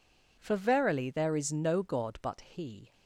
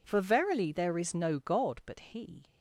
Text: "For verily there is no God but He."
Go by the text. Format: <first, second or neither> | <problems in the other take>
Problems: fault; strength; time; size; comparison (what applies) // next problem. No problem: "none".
neither | none